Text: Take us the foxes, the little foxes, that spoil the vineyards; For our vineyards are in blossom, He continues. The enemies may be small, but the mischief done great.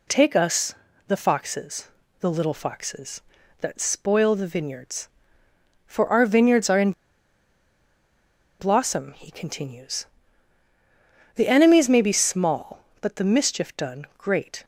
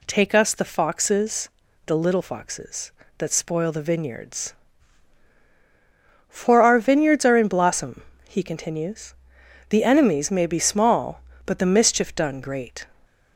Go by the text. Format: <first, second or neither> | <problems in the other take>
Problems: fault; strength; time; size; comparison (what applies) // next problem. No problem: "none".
second | pauses between "us" and "the"; slight; at 0.7 s; 0.34 s long // pauses between "in" and "blossom"; strong; at 6.9 s; 1.6 s long